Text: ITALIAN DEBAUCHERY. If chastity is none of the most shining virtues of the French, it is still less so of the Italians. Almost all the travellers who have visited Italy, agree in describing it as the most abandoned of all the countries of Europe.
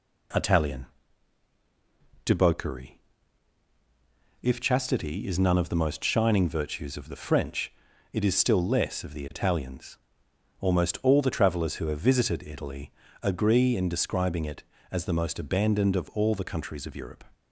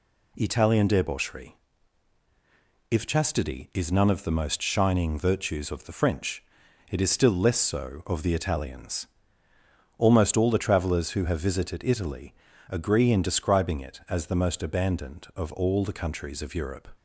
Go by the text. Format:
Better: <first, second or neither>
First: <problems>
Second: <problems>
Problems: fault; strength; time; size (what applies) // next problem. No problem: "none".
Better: second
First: pauses between "ITALIAN" and "DEBAUCHERY"; strong; at 0.8 s; 1.3 s long // skips "so"; at 9.0 s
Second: none